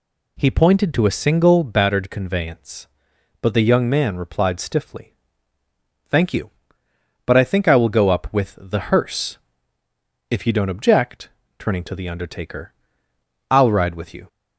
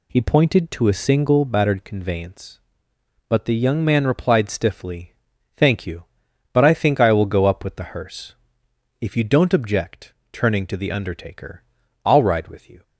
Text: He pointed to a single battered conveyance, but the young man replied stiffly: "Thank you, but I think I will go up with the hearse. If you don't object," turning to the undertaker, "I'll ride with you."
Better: neither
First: none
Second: none

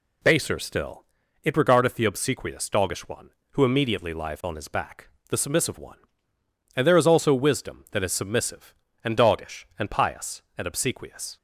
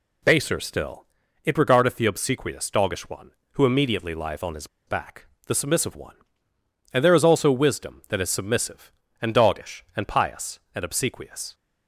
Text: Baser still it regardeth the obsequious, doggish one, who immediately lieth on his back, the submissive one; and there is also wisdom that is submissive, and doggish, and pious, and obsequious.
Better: first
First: pauses between "still" and "it"; at 1.0 s; 0.40 s long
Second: pauses between "still" and "it"; at 1.0 s; 0.40 s long // pauses between "his" and "back"; slight; at 4.6 s; 0.21 s long

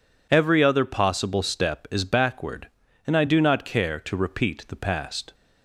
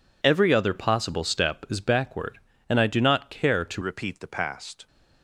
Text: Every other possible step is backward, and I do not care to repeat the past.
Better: first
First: none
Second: changes voice at "repeat"; from 3.8 s on; 1.0 s long

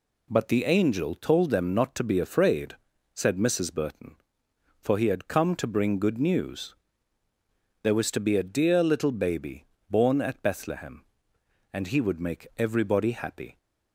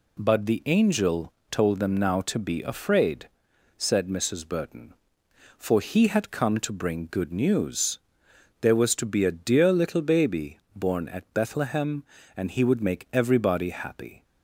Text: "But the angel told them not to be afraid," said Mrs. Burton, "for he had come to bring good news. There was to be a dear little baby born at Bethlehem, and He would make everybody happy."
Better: first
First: pauses between "baby" and "born"; slight; at 9.6 s; 0.24 s long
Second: pauses between "angel" and "told"; slight; at 1.3 s; 0.20 s long // says "now" for "not"; at 1.9 s // pauses between "baby" and "born"; slight; at 10.5 s; 0.16 s long

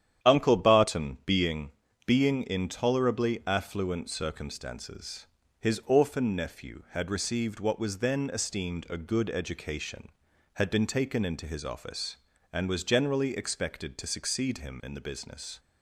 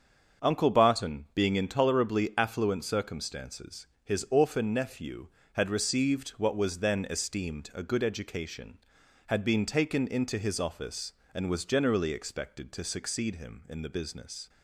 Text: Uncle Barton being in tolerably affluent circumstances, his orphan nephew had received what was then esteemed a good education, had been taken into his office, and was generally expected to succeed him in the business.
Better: second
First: starts louder than the rest; strong; until 1.3 s; 10 dB // says "being" twice; at 2.0 s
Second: starts louder than the rest; until 1.5 s; 7 dB

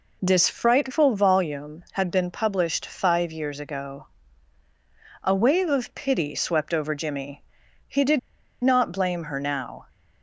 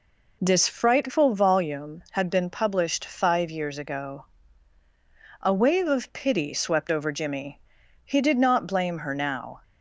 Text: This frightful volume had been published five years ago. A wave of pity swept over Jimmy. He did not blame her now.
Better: second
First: pauses between "did" and "not"; at 8.1 s; 0.42 s long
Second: none

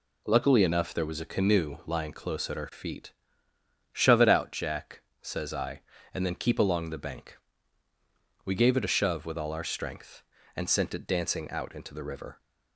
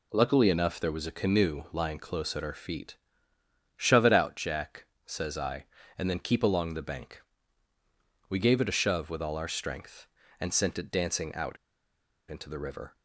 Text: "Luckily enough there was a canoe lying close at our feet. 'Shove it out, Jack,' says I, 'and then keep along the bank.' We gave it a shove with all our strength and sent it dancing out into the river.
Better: first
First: none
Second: pauses between "out" and "into"; noticeable; at 11.5 s; 0.74 s long

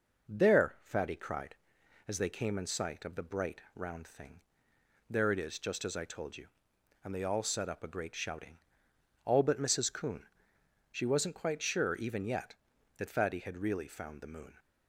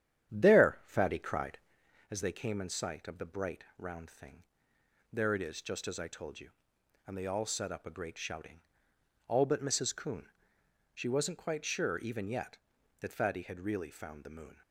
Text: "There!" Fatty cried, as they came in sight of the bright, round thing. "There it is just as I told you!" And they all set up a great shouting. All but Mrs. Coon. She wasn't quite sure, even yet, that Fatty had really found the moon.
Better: first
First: none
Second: starts louder than the rest; strong; until 1.9 s; 10 dB

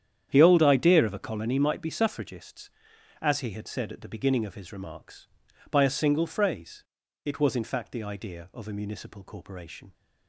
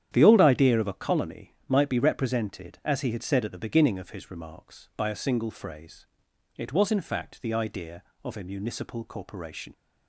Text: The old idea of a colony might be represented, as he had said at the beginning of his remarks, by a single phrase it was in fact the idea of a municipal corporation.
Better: second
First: starts louder than the rest; strong; until 1.3 s; 9.5 dB // says "suffragists" for "represented"; at 1.8 s // pauses between "phrase" and "it"; at 6.8 s; 0.42 s long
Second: starts louder than the rest; strong; until 1.1 s; 10 dB // pauses between "phrase" and "it"; noticeable; at 6.0 s; 0.48 s long

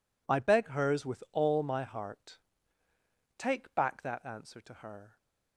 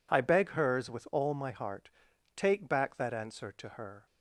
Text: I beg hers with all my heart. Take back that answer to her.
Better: neither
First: none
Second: none

